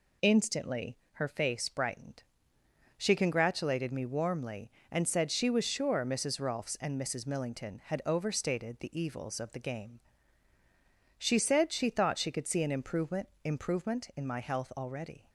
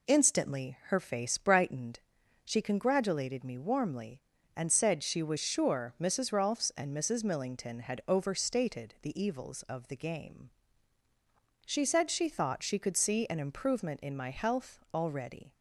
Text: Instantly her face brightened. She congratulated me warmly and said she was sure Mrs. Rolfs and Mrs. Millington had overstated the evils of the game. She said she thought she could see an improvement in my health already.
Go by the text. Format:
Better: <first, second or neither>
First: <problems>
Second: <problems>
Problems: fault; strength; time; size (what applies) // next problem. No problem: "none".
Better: second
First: pauses between "Instantly" and "her"; slight; at 0.9 s; 0.16 s long // says "improvement" twice; at 13.4 s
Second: none